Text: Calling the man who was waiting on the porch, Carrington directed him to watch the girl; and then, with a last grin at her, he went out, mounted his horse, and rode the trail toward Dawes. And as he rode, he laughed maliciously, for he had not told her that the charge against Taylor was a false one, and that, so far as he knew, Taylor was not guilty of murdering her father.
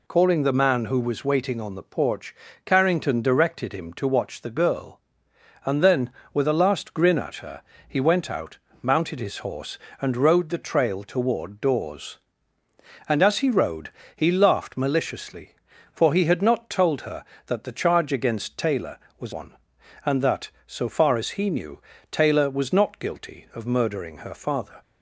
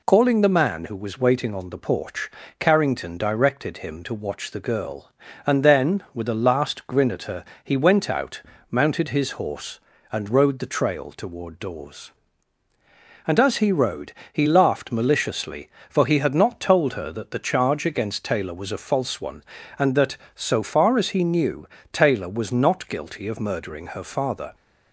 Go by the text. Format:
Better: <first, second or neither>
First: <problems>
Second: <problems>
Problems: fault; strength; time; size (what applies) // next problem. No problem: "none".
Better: second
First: skips "a false"; at 19.3 s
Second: none